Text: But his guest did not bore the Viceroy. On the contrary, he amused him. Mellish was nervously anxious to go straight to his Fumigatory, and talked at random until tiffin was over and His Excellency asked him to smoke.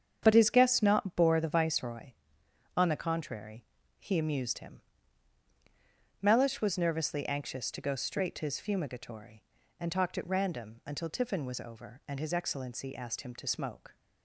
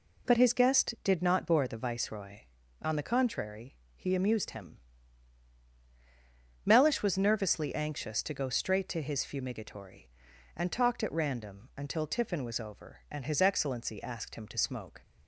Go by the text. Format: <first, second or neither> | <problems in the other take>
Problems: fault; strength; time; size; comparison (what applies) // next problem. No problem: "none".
second | starts louder than the rest; strong; until 1.2 s; 7.5 dB // skips "did"; at 0.8 s